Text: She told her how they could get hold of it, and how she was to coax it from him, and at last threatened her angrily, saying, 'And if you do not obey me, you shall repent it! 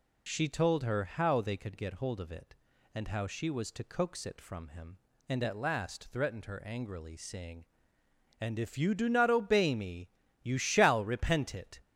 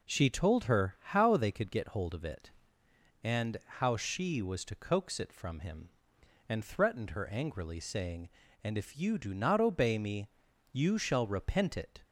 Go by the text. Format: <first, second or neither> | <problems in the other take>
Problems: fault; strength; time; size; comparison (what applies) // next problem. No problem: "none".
first | pauses between "and" and "how"; slight; at 3.5 s; 0.22 s long // skips "at last"; at 6.6 s